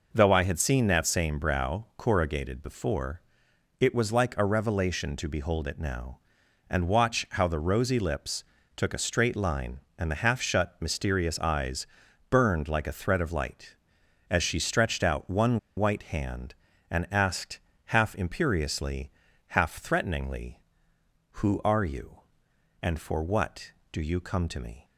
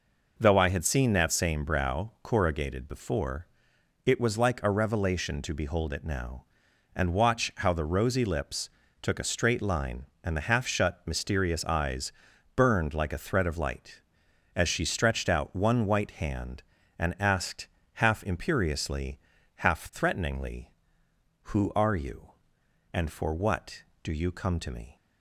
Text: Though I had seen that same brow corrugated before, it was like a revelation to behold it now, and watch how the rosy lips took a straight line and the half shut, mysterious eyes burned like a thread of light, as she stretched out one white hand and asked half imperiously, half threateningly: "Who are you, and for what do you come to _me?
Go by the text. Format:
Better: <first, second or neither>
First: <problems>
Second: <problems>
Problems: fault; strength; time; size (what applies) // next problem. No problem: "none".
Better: second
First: pauses between "lips" and "took"; slight; at 8.4 s; 0.32 s long // pauses between "eyes" and "burned"; at 11.8 s; 0.42 s long // pauses between "one" and "white"; slight; at 15.5 s; 0.18 s long // pauses between "asked" and "half"; slight; at 17.5 s; 0.28 s long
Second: pauses between "lips" and "took"; slight; at 8.6 s; 0.32 s long // pauses between "eyes" and "burned"; at 12.1 s; 0.42 s long // pauses between "asked" and "half"; slight; at 17.6 s; 0.28 s long